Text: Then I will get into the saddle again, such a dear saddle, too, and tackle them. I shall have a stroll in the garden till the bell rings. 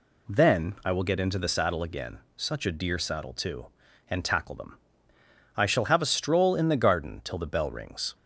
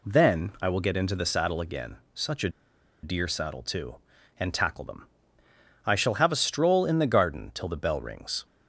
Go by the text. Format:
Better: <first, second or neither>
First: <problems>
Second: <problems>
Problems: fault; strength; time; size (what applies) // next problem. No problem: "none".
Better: first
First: none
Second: pauses between "a" and "dear"; noticeable; at 2.4 s; 0.53 s long